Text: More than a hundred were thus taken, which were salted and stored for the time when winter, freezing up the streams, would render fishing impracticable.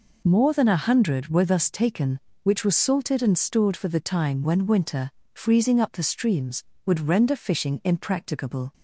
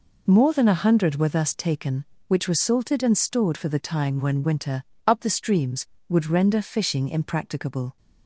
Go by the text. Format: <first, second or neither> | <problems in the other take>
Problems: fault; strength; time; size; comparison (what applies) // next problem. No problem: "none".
first | skips "freezing"; at 4.9 s